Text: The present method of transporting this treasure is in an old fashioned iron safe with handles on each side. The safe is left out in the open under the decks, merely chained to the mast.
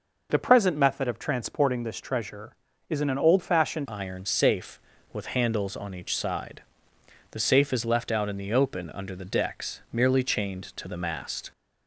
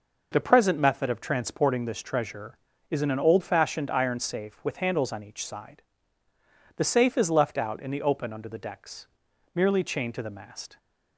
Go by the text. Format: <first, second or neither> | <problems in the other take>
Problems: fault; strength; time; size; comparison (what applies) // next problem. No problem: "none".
second | changes voice at "iron"; from 3.8 s on; 7.7 s long